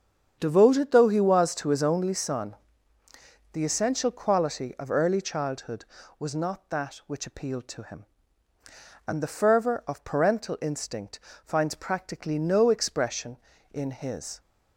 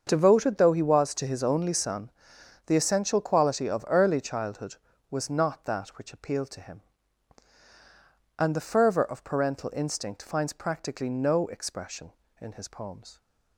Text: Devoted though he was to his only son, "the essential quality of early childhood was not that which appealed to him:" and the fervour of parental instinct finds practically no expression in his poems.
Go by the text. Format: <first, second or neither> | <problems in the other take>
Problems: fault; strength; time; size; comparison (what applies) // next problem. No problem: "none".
second | starts louder than the rest; strong; until 1.4 s; 8 dB; also in the second // pauses between "instinct" and "finds"; slight; at 11.1 s; 0.24 s long // stops before "poems"; at 14.3 s